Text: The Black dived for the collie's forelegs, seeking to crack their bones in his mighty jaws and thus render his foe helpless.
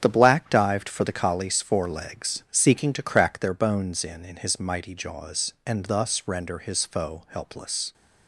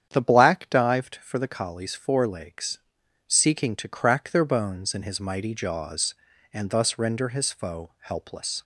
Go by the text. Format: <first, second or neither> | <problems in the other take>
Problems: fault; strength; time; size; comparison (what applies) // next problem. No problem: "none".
second | starts louder than the rest; strong; until 1.0 s; 8 dB; strong in the second // says "in" twice; at 4.2 s